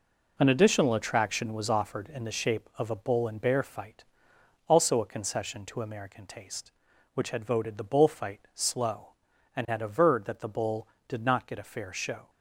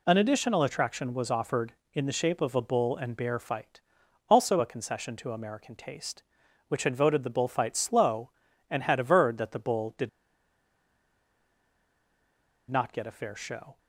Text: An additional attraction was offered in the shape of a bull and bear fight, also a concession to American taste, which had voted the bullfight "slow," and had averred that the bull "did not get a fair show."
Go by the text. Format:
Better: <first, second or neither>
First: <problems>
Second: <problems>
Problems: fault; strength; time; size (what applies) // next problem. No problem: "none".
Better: first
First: none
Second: pauses between "did" and "not"; strong; at 10.0 s; 2.6 s long